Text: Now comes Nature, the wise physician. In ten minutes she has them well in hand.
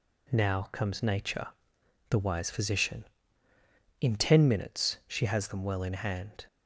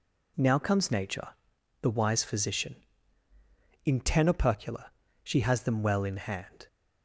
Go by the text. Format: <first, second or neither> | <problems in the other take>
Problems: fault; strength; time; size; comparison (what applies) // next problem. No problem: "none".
first | says "opercula" for "minutes"; at 4.2 s